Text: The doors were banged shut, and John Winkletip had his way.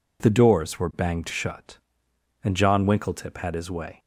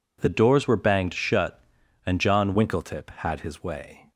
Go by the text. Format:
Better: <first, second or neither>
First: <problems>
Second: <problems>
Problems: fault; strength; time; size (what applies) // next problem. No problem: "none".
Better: first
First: none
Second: changes voice from "doors" to "John"; from 0.2 to 2.5 s; 2.3 s long